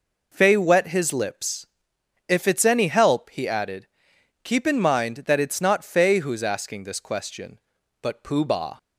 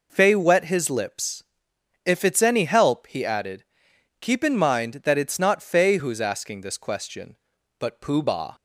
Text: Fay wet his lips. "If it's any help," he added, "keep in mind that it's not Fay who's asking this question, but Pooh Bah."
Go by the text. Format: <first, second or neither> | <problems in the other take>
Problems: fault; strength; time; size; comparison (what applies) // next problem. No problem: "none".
neither | none